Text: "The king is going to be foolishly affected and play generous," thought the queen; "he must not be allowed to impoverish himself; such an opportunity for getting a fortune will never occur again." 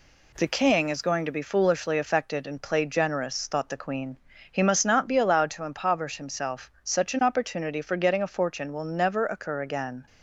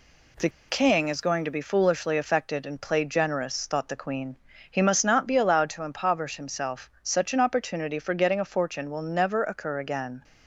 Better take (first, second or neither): first